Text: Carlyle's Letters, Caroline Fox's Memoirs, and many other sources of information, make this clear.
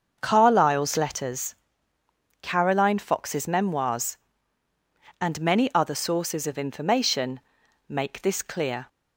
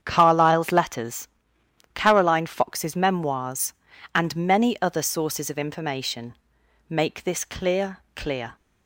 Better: first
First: starts louder than the rest; until 1.2 s; 7 dB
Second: starts louder than the rest; strong; until 1.0 s; 8.5 dB // says "clear" twice; at 8.1 s

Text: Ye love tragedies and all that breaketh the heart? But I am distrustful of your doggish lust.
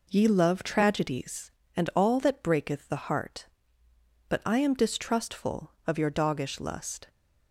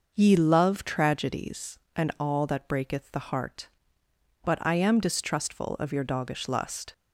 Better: neither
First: none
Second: none

